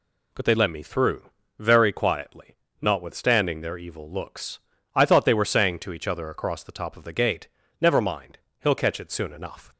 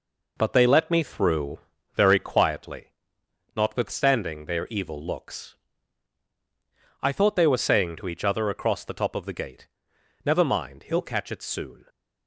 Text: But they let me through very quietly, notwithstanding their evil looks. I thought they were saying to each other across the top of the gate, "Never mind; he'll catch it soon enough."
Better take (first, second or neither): first